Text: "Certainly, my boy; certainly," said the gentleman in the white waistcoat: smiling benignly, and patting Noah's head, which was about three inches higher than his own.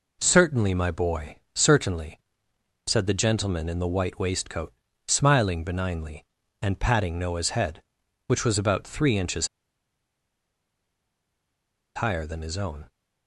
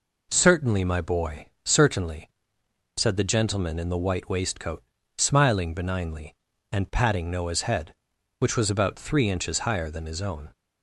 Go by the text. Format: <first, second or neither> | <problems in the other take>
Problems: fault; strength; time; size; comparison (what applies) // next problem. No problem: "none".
second | pauses between "inches" and "higher"; strong; at 9.4 s; 2.4 s long